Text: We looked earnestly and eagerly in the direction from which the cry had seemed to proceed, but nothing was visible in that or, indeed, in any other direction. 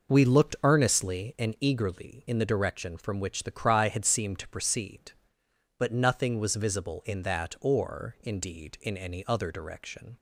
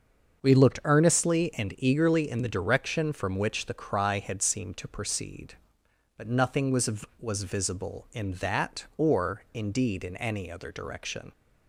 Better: first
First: none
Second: starts louder than the rest; until 1.4 s; 6.5 dB // says "was" twice; at 7.1 s

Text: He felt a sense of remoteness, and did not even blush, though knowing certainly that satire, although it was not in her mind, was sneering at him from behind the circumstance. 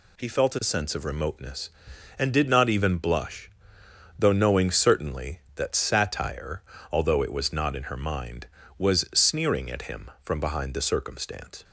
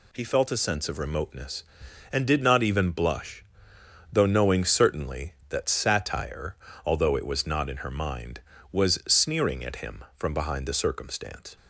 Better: neither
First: none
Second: none

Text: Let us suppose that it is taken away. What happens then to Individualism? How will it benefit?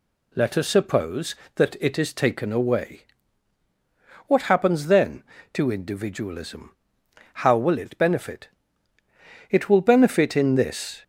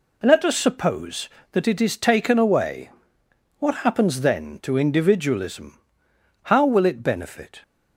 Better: second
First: goes on to say "It will benefit in this"; from 9.4 s on; 1.5 s long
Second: none

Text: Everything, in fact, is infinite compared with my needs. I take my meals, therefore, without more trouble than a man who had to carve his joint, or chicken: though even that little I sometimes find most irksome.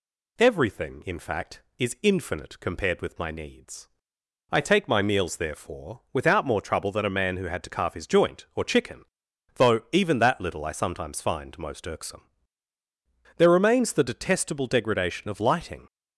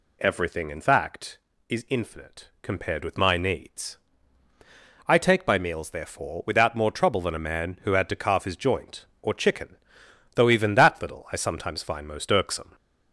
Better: second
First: goes on to say "There remains the detestable degradation of lighting"; strong; from 13.3 s on; 2.5 s long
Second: none

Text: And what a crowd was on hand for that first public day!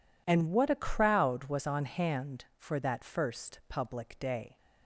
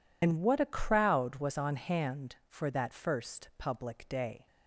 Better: first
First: none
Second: loses the start of "And"; at 0.2 s; 60 ms

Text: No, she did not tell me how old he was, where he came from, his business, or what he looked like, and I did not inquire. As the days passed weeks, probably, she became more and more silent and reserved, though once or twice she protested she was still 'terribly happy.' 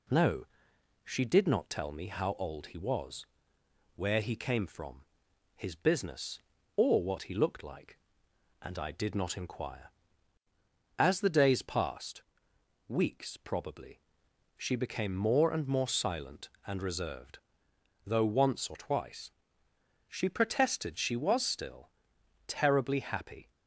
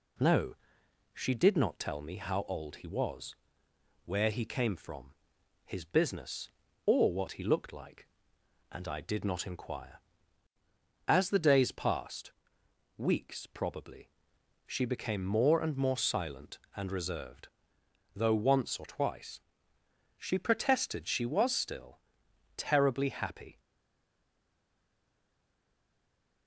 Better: first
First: pauses between "passed" and "weeks"; noticeable; at 12.2 s; 0.66 s long // pauses between "twice" and "she"; noticeable; at 19.2 s; 0.80 s long // pauses between "still" and "terribly"; noticeable; at 21.8 s; 0.56 s long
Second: pauses between "passed" and "weeks"; noticeable; at 12.3 s; 0.66 s long // pauses between "twice" and "she"; noticeable; at 19.3 s; 0.80 s long // pauses between "still" and "terribly"; noticeable; at 21.9 s; 0.56 s long // stays silent after the last word; strong; from 23.5 s on; 2.9 s long

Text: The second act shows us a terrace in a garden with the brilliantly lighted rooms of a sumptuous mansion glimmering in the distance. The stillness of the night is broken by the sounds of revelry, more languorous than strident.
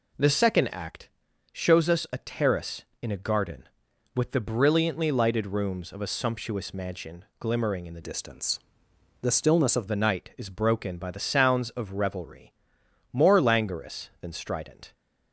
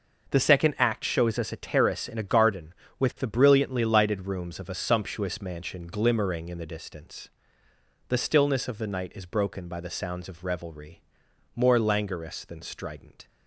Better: second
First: pauses between "act" and "shows"; at 1.0 s; 0.42 s long // pauses between "mansion" and "glimmering"; slight; at 7.2 s; 0.16 s long // changes voice from "distance" to "of"; from 8.0 to 9.8 s; 1.8 s long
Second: none

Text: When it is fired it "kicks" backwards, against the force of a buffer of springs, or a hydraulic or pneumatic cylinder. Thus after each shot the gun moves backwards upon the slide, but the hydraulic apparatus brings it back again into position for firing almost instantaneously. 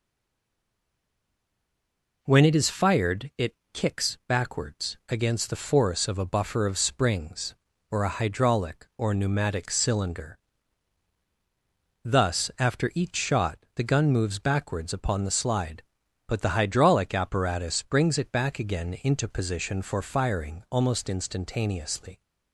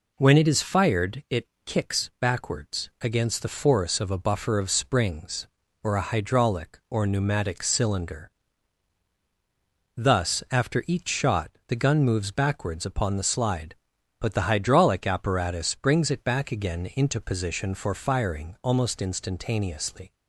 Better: second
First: stays silent before the first word; until 2.2 s; 2.2 s long // pauses between "it" and "kicks"; slight; at 3.5 s; 0.18 s long // pauses between "shot" and "the"; slight; at 13.5 s; 0.16 s long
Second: pauses between "it" and "kicks"; slight; at 1.4 s; 0.18 s long // pauses between "shot" and "the"; slight; at 11.4 s; 0.16 s long

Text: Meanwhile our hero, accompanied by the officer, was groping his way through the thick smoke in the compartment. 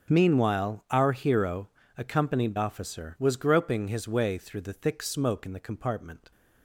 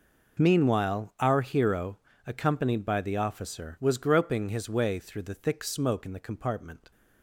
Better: second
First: skips "by the"; at 2.5 s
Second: none

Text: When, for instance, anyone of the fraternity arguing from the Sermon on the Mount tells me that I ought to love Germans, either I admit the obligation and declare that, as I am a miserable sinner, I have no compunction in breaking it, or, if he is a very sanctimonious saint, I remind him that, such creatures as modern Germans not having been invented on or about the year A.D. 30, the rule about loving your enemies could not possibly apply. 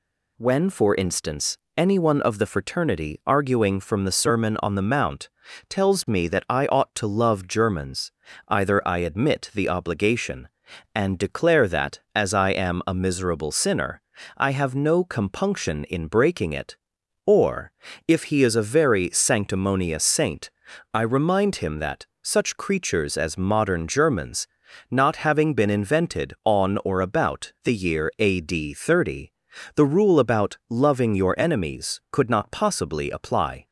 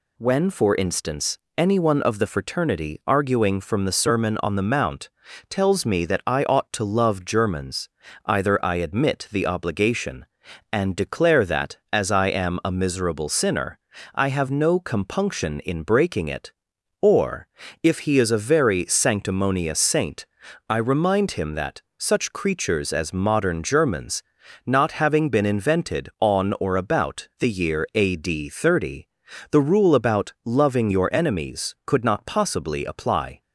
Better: neither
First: pauses between "Mount" and "tells"; at 5.2 s; 0.40 s long // pauses between "Germans" and "not"; at 24.4 s; 0.44 s long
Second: pauses between "Mount" and "tells"; at 5.0 s; 0.40 s long // pauses between "Germans" and "not"; at 24.2 s; 0.44 s long

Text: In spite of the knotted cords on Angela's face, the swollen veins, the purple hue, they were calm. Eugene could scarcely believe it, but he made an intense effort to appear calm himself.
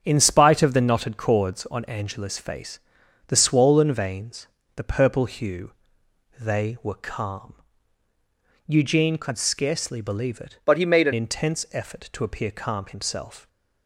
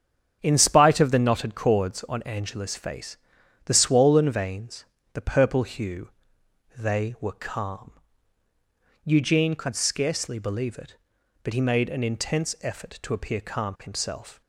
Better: second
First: starts louder than the rest; strong; until 1.0 s; 7 dB // changes voice from "but" to "an"; from 10.6 to 11.1 s; 0.5 s long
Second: starts louder than the rest; strong; until 1.4 s; 7.5 dB

